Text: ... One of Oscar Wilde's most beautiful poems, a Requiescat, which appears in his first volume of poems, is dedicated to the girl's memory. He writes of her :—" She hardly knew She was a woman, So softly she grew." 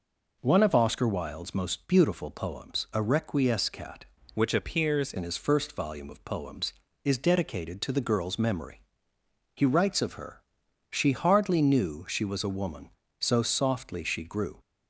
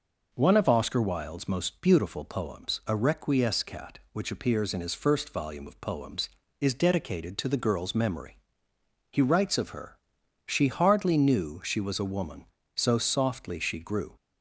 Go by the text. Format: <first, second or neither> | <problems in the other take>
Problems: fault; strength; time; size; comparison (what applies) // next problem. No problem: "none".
second | changes voice from "which" to "appears"; from 4.3 to 5.1 s; 0.8 s long